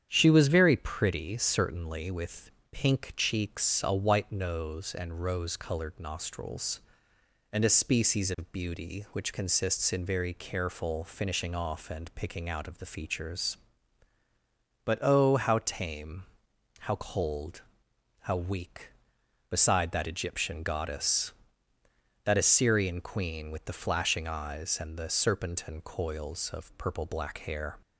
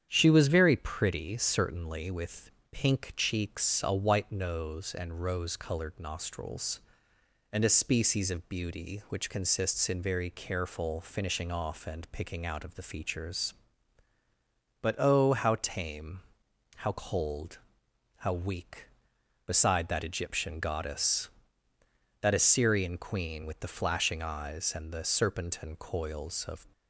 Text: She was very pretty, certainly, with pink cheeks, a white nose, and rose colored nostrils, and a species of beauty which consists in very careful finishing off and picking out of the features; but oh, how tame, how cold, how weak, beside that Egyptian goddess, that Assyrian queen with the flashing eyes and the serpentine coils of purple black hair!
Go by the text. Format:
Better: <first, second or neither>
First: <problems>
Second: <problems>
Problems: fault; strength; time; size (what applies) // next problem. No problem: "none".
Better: first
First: starts louder than the rest; strong; until 1.1 s; 9 dB // pauses between "with" and "pink"; slight; at 2.4 s; 0.22 s long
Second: starts louder than the rest; strong; until 1.1 s; 9 dB // pauses between "with" and "pink"; slight; at 2.4 s; 0.22 s long // stops before "purple black hair"; at 26.7 s